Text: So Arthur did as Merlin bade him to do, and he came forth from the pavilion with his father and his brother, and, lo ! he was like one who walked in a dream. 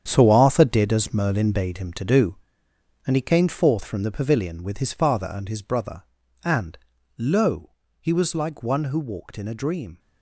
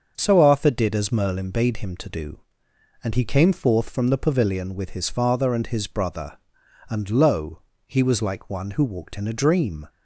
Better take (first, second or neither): second